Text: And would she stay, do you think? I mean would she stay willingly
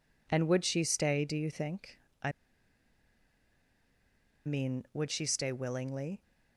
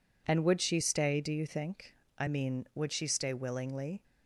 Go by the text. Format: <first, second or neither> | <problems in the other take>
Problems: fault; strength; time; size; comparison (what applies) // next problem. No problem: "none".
second | pauses between "I" and "mean"; strong; at 2.3 s; 2.1 s long